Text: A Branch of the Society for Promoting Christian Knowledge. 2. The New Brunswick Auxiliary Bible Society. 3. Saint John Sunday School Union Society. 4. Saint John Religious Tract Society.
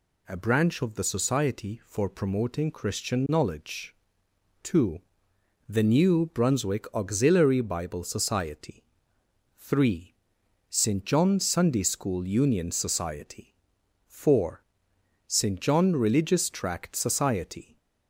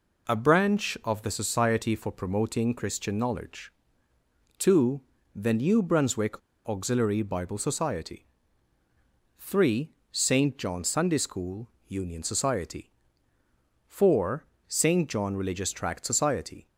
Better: first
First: none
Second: pauses between "Brunswick" and "Auxiliary"; slight; at 6.4 s; 0.27 s long // pauses between "School" and "Union"; slight; at 11.6 s; 0.20 s long

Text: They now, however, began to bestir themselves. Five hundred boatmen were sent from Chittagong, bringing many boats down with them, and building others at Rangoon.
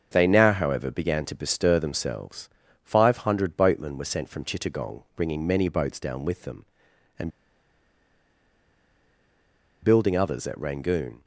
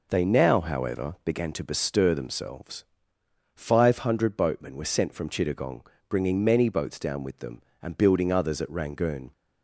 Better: second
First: starts louder than the rest; until 1.1 s; 7 dB // pauses between "and" and "building"; strong; at 7.3 s; 2.5 s long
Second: none

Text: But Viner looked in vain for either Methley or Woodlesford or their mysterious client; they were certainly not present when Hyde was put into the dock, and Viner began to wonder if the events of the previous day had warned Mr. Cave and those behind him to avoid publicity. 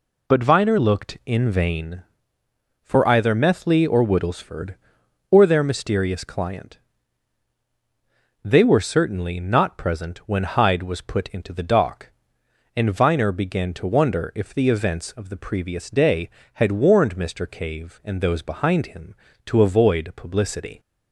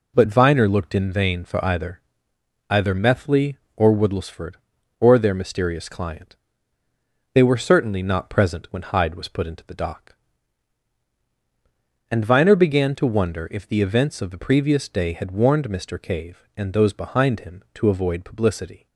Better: first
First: none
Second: says "either" twice; at 2.7 s

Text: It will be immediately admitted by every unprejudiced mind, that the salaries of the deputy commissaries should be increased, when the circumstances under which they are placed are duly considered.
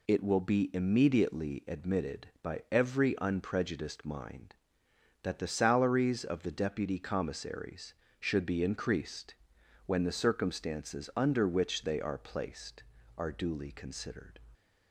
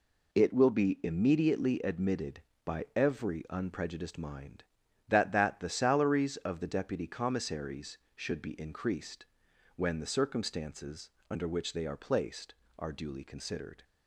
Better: first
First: none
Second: says "that" twice; at 5.3 s // pauses between "circumstances" and "under"; slight; at 11.0 s; 0.20 s long

